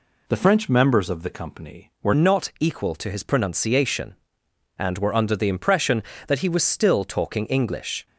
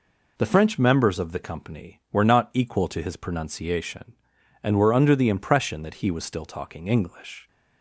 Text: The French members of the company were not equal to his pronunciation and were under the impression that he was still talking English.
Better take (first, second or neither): second